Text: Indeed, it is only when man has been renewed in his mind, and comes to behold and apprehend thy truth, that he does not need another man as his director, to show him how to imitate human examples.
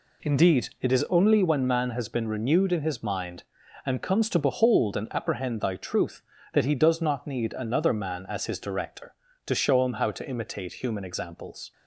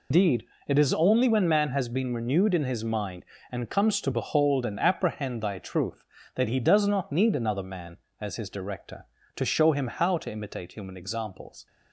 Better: first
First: none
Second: loses the start of "Indeed"; at 0.1 s; 165 ms

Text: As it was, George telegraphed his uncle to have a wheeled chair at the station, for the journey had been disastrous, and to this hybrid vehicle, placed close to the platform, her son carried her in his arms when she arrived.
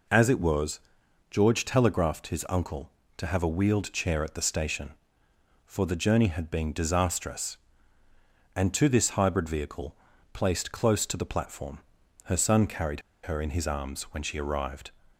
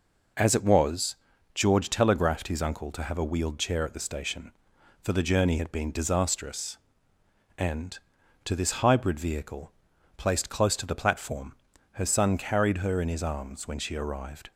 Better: second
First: pauses between "carried" and "her"; slight; at 13.0 s; 0.22 s long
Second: none

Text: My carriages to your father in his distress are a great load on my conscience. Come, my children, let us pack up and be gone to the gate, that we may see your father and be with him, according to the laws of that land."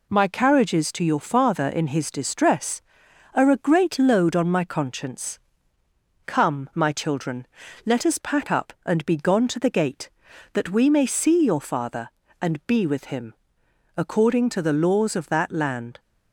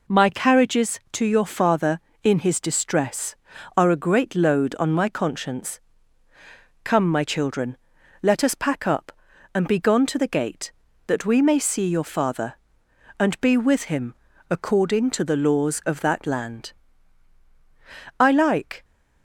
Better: first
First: none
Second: goes on to say "I like"; noticeable; from 18.2 s on; 0.64 s long

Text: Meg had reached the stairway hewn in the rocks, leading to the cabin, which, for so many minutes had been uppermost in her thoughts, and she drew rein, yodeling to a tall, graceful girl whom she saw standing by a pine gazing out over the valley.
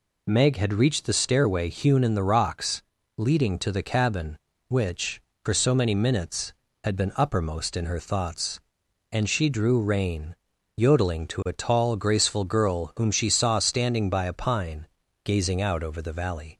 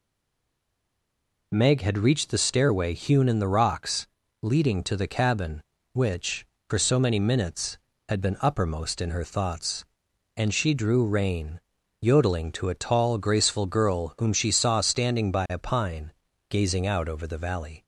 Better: first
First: pauses between "pine" and "gazing"; at 14.8 s; 0.38 s long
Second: stays silent before the first word; noticeable; until 1.5 s; 1.5 s long // pauses between "pine" and "gazing"; at 16.1 s; 0.38 s long

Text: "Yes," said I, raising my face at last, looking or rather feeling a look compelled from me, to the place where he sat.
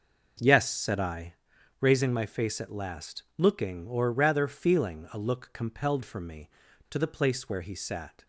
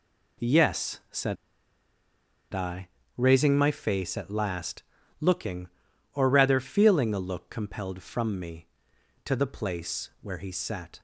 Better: first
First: none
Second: pauses between "said" and "I"; at 1.3 s; 1.1 s long

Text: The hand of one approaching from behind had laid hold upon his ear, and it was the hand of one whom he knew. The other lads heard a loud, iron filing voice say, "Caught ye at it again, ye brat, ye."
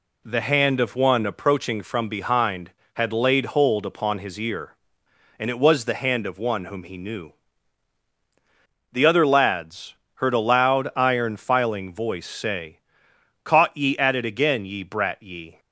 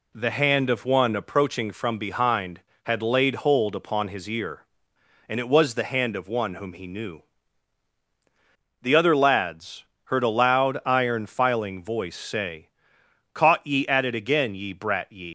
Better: first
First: pauses between "lads" and "heard"; slight; at 9.9 s; 0.20 s long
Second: pauses between "lads" and "heard"; slight; at 9.8 s; 0.20 s long // leaves "ye" unfinished; at 15.2 s; 155 ms

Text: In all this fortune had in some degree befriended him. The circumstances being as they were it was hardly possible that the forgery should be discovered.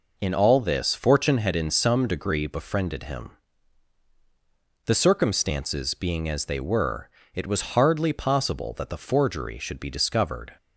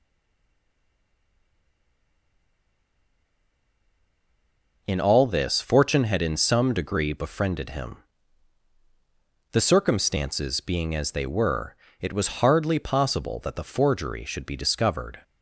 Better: first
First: pauses between "were" and "it"; slight; at 7.0 s; 0.26 s long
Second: stays silent before the first word; strong; until 4.8 s; 4.8 s long // pauses between "were" and "it"; slight; at 11.7 s; 0.26 s long

